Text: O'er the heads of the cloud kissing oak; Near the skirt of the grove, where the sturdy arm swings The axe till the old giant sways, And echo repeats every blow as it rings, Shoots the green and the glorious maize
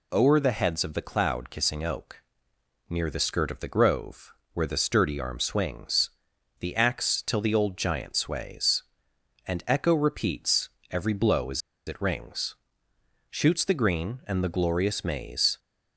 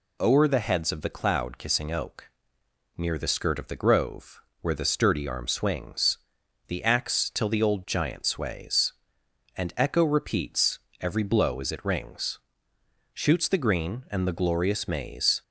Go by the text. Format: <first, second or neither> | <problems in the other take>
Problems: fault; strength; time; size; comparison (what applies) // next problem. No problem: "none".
second | pauses between "swings" and "The"; noticeable; at 6.1 s; 0.50 s long; noticeable in the second // pauses between "repeats" and "every"; slight; at 10.6 s; 0.24 s long; slight in the second // pauses between "as" and "it"; slight; at 11.6 s; 0.26 s long